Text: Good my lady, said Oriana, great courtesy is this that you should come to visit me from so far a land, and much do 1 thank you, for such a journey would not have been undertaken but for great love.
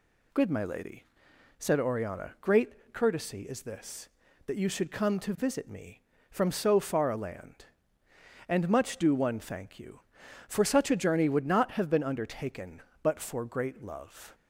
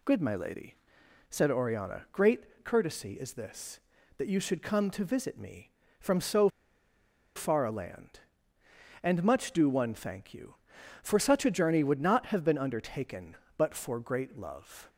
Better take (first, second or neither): first